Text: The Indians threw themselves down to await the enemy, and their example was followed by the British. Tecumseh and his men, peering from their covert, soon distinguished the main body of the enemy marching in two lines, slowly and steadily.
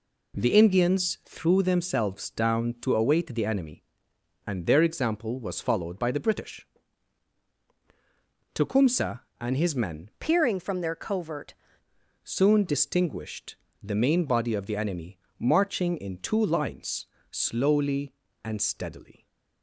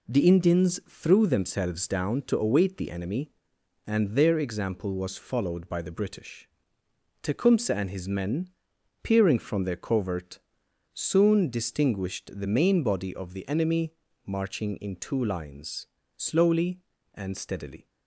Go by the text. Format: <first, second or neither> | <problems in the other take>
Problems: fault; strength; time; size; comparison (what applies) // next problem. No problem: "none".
second | changes voice from "peering" to "covert"; from 10.1 to 11.5 s; 1.4 s long // pauses between "distinguished" and "the"; slight; at 13.5 s; 0.26 s long // pauses between "enemy" and "marching"; slight; at 15.1 s; 0.22 s long; slight in the second